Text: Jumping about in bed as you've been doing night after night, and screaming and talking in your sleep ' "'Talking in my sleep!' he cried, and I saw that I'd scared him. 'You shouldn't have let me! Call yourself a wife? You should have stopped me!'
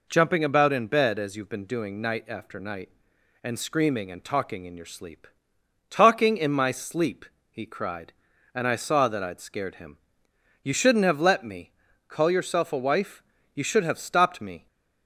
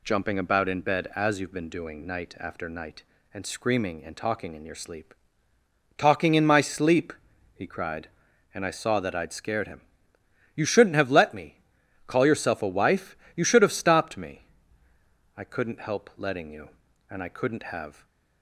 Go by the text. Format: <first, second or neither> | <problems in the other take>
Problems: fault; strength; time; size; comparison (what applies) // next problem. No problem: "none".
first | goes on to say "I couldn't help letting you and I couldn't have"; strong; from 15.3 s on; 2.6 s long // stays silent after the last word; slight; from 17.9 s on; 0.5 s long